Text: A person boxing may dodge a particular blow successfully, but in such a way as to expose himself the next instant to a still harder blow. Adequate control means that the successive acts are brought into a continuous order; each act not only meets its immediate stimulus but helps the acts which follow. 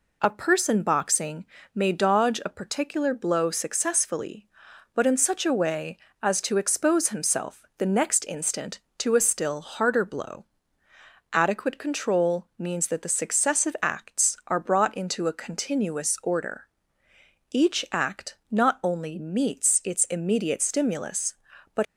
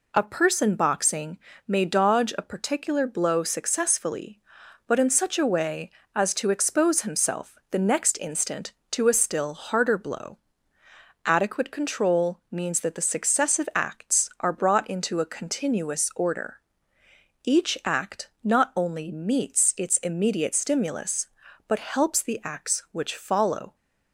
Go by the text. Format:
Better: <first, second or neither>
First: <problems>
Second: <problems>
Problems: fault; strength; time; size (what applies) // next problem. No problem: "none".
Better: second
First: pauses between "boxing" and "may"; slight; at 1.4 s; 0.30 s long // stops before "helps the acts which follow"; at 21.8 s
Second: pauses between "boxing" and "may"; slight; at 1.3 s; 0.30 s long